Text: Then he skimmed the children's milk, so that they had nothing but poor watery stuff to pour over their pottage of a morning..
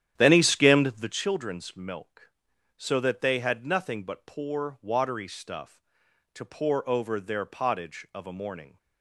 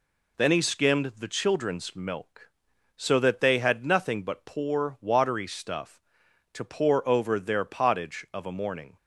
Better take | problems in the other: second | starts louder than the rest; strong; until 1.3 s; 10.5 dB

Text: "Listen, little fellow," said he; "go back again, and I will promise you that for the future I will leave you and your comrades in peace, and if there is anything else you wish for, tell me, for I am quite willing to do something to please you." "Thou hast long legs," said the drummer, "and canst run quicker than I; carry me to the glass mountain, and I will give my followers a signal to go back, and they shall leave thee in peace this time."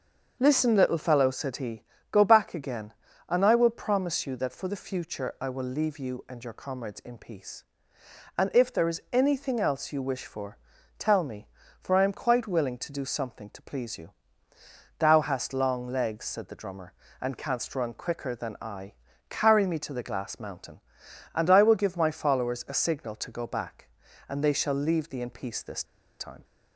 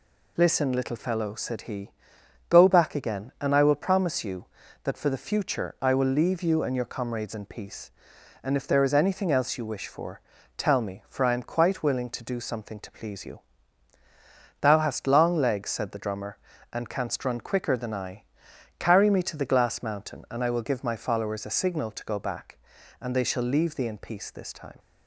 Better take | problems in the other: second | starts louder than the rest; until 1.4 s; 6.5 dB // pauses between "this" and "time"; slight; at 25.8 s; 0.35 s long

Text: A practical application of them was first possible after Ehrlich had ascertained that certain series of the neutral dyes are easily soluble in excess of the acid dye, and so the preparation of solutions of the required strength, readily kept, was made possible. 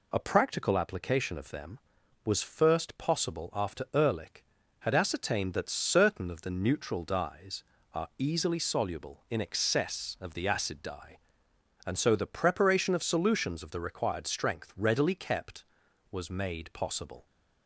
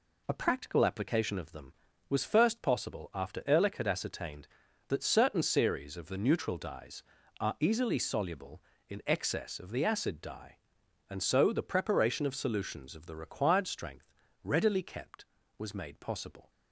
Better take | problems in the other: second | skips "series"; at 6.2 s

